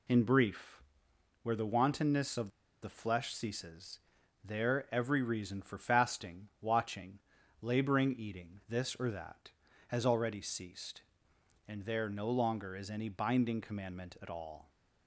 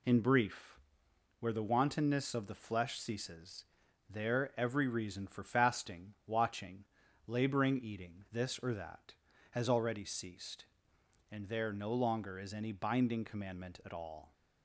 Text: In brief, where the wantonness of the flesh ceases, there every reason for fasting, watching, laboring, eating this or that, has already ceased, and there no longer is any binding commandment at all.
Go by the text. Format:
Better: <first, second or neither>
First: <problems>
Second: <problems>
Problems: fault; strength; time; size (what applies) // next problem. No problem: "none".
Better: second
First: pauses between "of" and "the"; slight; at 2.4 s; 0.34 s long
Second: none